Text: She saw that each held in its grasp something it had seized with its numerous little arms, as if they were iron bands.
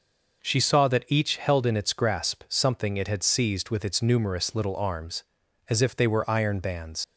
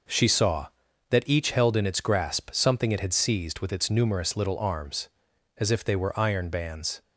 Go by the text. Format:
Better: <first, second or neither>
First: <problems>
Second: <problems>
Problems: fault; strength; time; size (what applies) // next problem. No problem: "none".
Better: second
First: leaves "bands" unfinished; at 7.0 s; 75 ms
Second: none